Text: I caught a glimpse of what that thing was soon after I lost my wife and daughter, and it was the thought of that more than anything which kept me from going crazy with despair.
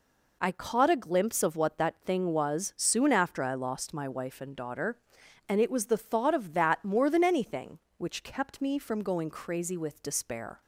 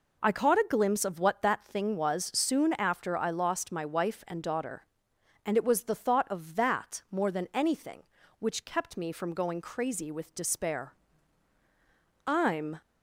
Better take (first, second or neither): first